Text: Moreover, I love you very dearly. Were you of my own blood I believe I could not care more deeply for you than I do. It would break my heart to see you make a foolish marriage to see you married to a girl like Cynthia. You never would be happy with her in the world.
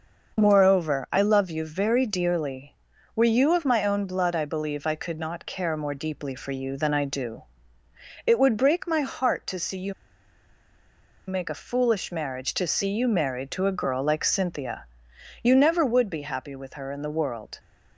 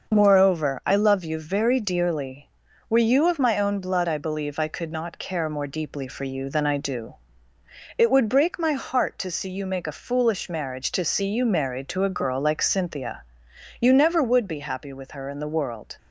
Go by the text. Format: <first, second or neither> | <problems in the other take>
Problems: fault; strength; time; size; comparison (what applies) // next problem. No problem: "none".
second | starts louder than the rest; noticeable; until 1.4 s; 6 dB; noticeable in the second // pauses between "you" and "make"; strong; at 9.9 s; 1.3 s long